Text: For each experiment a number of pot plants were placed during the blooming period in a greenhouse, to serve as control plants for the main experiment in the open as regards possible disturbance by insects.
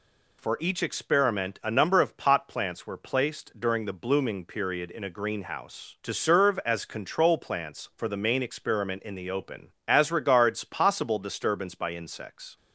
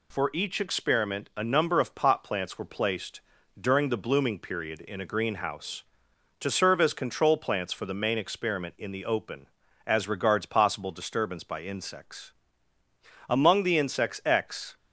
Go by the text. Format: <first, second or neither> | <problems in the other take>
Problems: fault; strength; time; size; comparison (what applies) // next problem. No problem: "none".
first | pauses between "placed" and "during"; at 3.2 s; 0.38 s long // goes on to say "Among the insects x"; from 13.2 s on; 1.4 s long